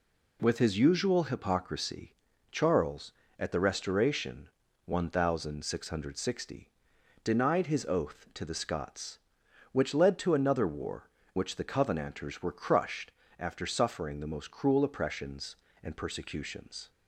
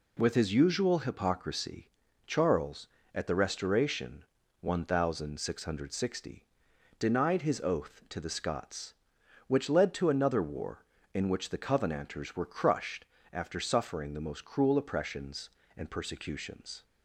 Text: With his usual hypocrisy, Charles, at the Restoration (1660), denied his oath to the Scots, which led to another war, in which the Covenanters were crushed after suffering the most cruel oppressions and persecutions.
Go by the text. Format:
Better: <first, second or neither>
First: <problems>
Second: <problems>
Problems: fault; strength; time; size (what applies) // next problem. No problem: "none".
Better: second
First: skips "in"; at 11.2 s // pauses between "crushed" and "after"; slight; at 13.1 s; 0.26 s long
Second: pauses between "crushed" and "after"; slight; at 13.0 s; 0.26 s long